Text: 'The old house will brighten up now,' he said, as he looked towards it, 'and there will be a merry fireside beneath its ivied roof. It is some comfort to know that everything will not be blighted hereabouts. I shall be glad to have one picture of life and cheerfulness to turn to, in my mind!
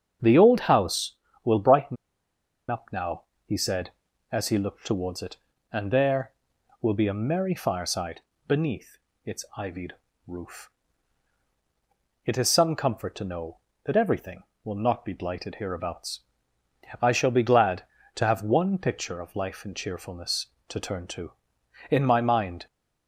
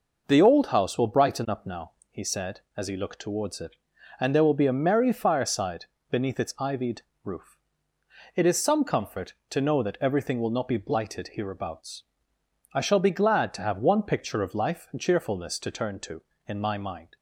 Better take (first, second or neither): second